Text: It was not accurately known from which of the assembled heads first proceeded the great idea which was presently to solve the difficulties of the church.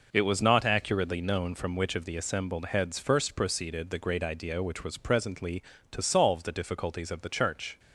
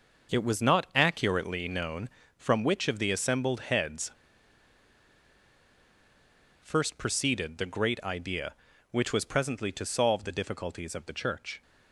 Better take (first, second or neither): first